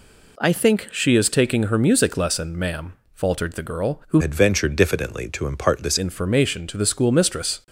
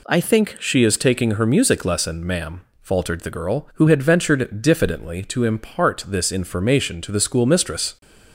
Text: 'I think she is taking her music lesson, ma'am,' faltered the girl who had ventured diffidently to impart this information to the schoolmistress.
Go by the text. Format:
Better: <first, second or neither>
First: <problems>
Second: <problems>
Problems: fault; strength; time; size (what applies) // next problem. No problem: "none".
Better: second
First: changes voice from "had" to "this"; from 4.2 to 5.9 s; 1.7 s long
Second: none